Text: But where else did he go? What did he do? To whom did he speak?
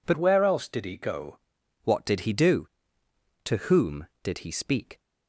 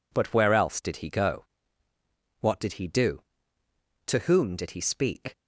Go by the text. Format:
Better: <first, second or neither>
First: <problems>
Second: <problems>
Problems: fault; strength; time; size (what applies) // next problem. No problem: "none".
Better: second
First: changes voice from "where" to "go"; from 0.1 to 1.3 s; 1.2 s long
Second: none